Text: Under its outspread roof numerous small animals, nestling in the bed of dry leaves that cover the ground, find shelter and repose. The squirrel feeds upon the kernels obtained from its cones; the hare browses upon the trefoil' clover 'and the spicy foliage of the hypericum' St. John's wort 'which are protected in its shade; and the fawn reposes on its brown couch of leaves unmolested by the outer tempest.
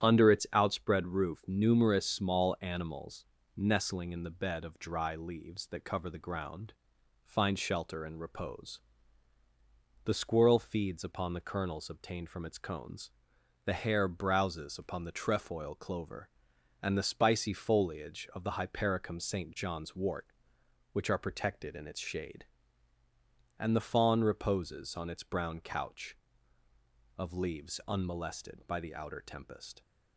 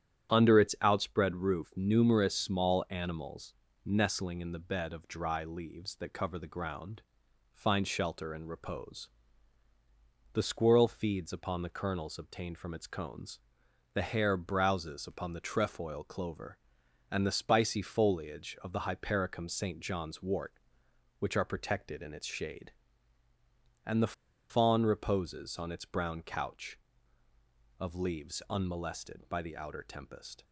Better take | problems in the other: first | starts louder than the rest; strong; until 1.3 s; 9.5 dB; strong in the first // pauses between "the" and "fawn"; at 24.1 s; 0.37 s long

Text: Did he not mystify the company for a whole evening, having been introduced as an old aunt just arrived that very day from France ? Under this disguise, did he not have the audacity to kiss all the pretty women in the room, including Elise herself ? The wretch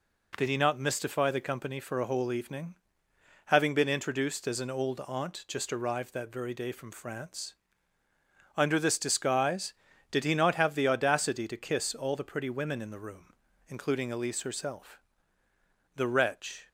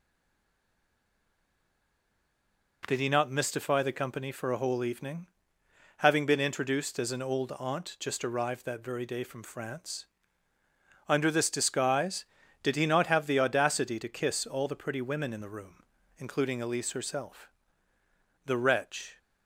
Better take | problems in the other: first | stays silent before the first word; strong; until 2.8 s; 2.8 s long

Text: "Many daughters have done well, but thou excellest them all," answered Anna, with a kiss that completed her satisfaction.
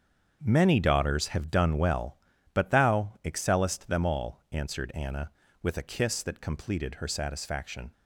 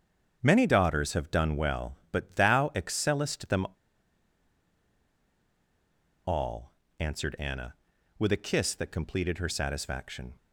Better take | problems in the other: first | starts louder than the rest; strong; until 1.4 s; 7.5 dB; strong in the first // pauses between "them" and "all"; strong; at 3.6 s; 2.5 s long

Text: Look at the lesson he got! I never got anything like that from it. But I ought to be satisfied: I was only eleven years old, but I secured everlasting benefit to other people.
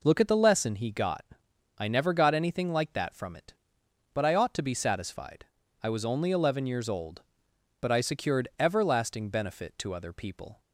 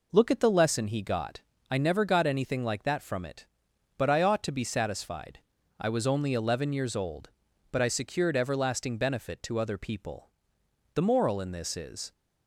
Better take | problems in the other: first | goes on to say "The moral in this is"; noticeable; from 10.9 s on; 1.1 s long

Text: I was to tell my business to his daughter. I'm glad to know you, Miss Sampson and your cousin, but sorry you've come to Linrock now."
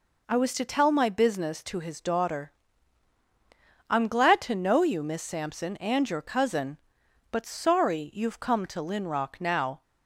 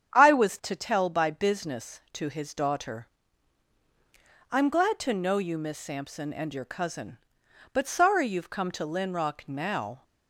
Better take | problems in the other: first | starts louder than the rest; strong; until 1.2 s; 8.5 dB // says "by" for "my"; at 1.0 s

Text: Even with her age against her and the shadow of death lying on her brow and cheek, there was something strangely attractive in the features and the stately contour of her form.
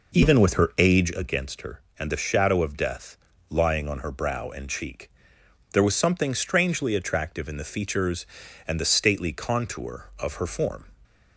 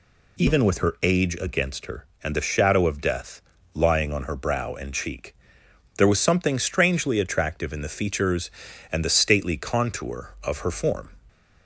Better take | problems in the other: second | starts louder than the rest; noticeable; until 1.2 s; 5 dB // pauses between "death" and "lying"; slight; at 3.1 s; 0.32 s long; slight in the second

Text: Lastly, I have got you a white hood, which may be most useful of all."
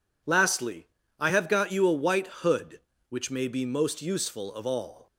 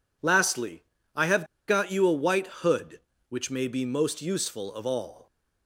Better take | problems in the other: first | pauses between "have" and "got"; slight; at 1.4 s; 0.23 s long

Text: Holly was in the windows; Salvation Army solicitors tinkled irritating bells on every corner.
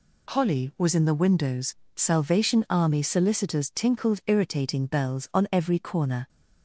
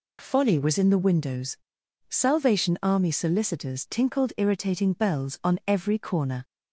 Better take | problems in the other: first | says "Folly" for "Holly"; at 0.1 s

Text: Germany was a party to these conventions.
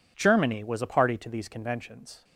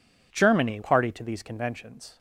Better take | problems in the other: first | skips "was a"; at 0.8 s

